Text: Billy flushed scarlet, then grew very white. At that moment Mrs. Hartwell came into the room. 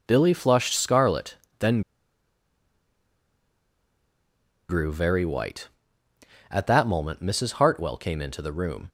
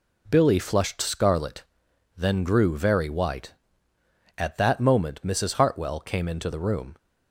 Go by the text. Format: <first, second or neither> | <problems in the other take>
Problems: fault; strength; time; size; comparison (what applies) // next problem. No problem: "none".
second | pauses between "then" and "grew"; strong; at 1.8 s; 2.8 s long